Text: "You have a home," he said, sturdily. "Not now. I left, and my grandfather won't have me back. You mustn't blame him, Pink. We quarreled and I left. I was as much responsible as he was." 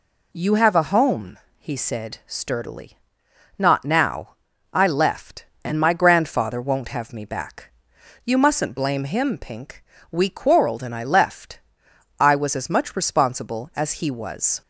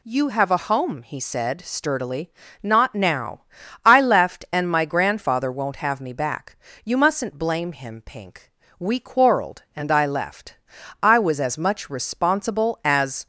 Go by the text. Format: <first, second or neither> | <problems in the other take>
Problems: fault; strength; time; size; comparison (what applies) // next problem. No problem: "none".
first | stops before "he was"; at 13.2 s